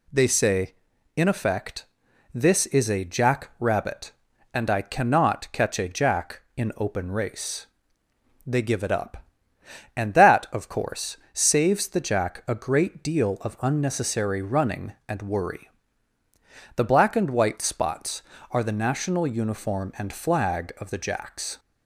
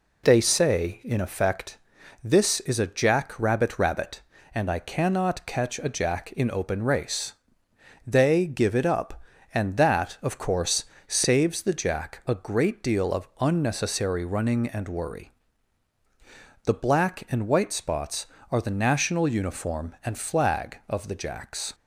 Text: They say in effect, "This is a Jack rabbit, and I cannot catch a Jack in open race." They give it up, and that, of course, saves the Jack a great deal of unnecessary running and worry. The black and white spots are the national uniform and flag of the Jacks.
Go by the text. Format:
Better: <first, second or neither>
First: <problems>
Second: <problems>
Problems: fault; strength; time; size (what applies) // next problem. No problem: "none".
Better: first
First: none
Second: says "rabbit" twice; at 3.7 s